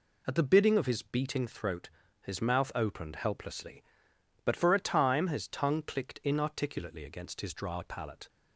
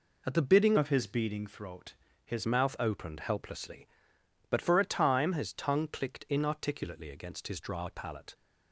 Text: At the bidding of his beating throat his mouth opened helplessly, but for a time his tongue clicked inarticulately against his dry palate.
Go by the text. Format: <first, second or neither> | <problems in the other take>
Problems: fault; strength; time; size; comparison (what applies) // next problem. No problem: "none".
first | changes voice from "of" to "his"; from 0.7 to 2.4 s; 1.7 s long // pauses between "throat" and "his"; slight; at 1.9 s; 0.30 s long; slight in the first